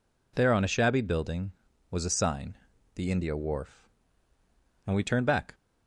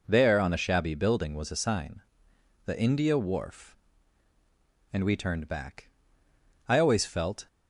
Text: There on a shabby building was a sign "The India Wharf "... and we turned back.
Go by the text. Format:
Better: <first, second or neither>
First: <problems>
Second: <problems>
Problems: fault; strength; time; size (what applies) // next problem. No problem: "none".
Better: first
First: pauses between "sign" and "The"; at 2.5 s; 0.40 s long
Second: pauses between "sign" and "The"; noticeable; at 2.0 s; 0.64 s long // goes on to say "I always felt"; noticeable; from 6.6 s on; 0.78 s long